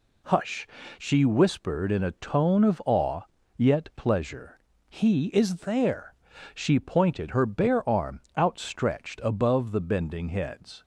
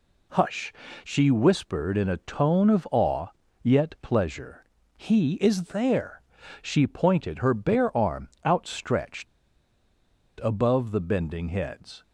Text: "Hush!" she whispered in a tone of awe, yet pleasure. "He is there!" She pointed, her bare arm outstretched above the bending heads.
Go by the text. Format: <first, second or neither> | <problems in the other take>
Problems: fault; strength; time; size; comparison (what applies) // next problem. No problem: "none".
first | pauses between "arm" and "outstretched"; slight; at 8.2 s; 0.18 s long; slight in the first // pauses between "outstretched" and "above"; at 9.2 s; 1.1 s long